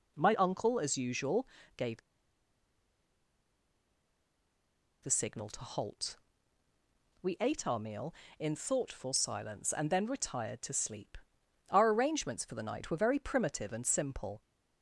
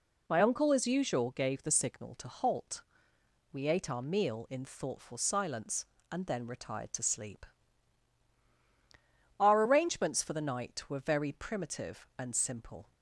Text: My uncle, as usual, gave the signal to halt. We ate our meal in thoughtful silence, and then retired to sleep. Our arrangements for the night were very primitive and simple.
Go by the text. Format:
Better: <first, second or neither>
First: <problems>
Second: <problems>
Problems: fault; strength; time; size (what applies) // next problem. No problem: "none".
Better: second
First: pauses between "gave" and "the"; strong; at 2.0 s; 3.0 s long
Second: none